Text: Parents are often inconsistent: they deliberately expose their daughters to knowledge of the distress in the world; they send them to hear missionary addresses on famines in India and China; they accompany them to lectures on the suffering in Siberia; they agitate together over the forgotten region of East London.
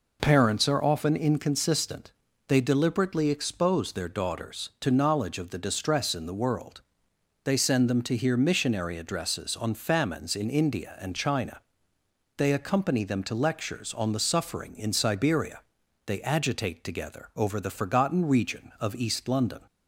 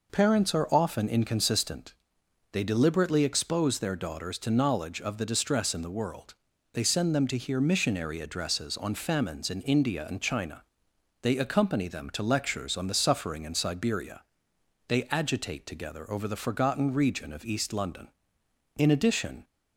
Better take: first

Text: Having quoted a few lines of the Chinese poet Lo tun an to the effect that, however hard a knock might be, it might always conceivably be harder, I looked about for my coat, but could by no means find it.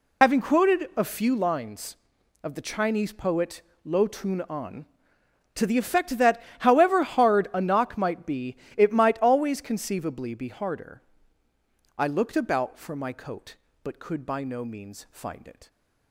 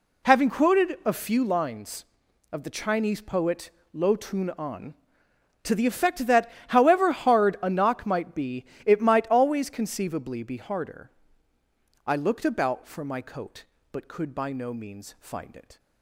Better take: second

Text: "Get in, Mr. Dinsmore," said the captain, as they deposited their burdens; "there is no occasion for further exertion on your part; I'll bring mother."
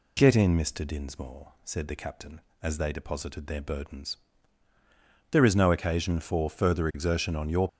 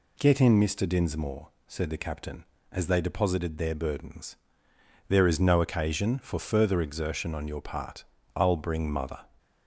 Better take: second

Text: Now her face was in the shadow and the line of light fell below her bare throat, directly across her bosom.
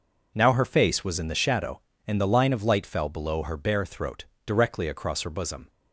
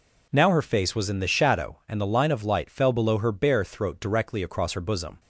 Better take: neither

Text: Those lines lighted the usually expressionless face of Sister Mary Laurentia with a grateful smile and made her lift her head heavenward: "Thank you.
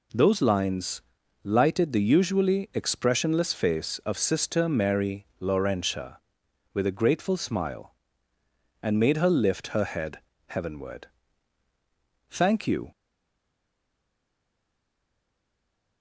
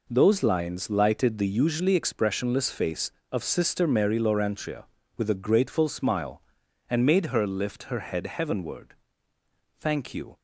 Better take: second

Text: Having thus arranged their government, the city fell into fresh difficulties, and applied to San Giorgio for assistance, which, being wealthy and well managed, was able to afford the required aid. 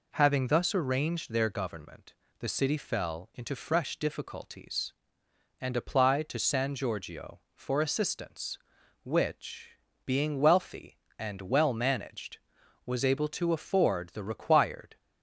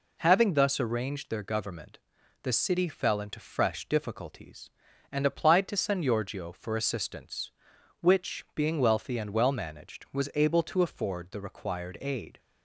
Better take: second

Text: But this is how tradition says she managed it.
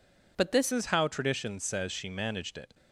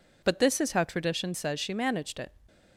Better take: second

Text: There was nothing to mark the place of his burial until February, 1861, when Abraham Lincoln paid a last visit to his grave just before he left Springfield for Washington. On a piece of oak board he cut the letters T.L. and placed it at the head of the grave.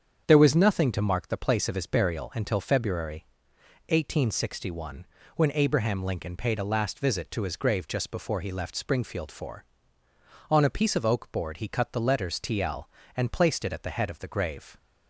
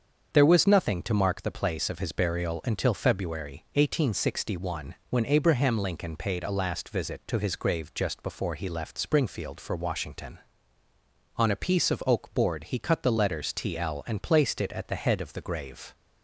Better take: second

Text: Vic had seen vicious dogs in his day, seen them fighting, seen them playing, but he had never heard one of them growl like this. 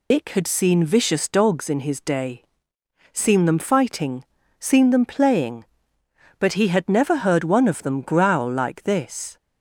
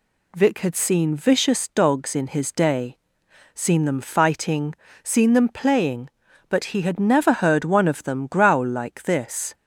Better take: second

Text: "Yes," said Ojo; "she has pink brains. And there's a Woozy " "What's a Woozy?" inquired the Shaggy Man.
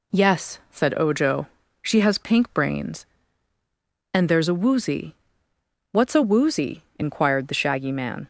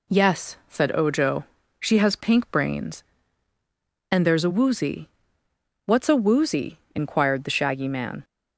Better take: neither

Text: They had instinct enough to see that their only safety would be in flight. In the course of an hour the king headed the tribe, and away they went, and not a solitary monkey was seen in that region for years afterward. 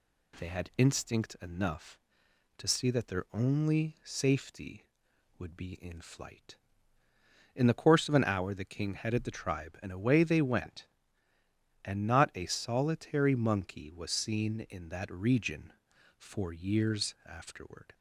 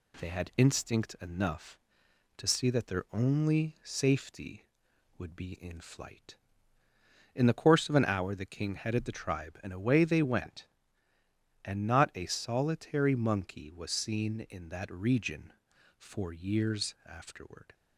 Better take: first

